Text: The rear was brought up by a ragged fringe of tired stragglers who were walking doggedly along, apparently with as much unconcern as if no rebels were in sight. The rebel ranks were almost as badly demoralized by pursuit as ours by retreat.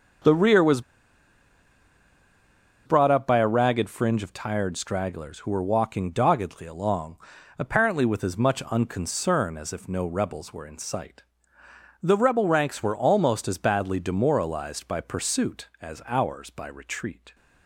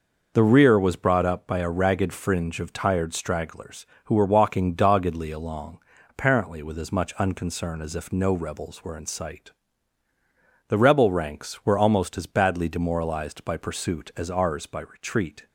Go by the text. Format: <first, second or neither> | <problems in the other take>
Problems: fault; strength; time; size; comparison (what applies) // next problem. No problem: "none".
second | starts louder than the rest; until 3.2 s; 6.5 dB // pauses between "was" and "brought"; strong; at 0.8 s; 2.0 s long